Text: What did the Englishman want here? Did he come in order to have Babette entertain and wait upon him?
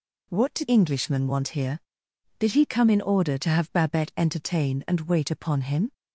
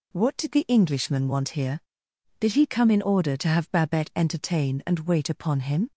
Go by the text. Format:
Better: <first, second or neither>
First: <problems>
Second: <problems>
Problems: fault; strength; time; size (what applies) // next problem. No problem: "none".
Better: second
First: skips "the"; at 0.6 s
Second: none